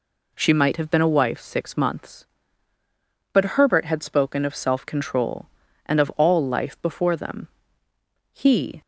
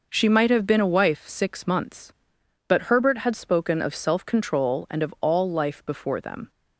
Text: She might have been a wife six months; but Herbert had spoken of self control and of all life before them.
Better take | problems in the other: second | goes on to say "He"; slight; from 8.3 s on; 0.48 s long

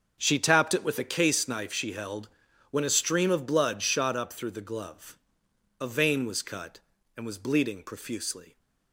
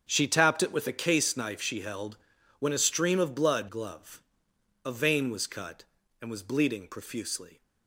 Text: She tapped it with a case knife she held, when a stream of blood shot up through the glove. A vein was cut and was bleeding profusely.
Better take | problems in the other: first | starts louder than the rest; strong; until 1.1 s; 8 dB; also in the first // skips "shot up through the"; at 3.6 s

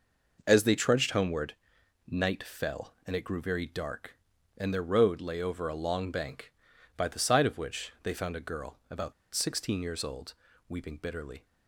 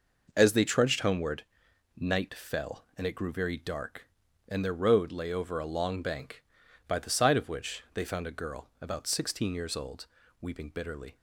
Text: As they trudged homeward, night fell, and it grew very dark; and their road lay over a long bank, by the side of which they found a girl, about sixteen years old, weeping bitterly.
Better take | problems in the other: second | pauses between "about" and "sixteen"; slight; at 9.1 s; 0.20 s long

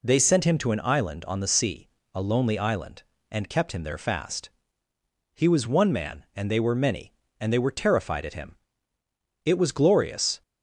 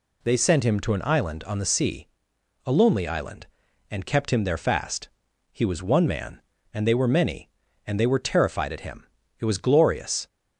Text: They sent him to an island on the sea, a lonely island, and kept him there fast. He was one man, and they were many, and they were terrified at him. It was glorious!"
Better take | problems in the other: neither | none

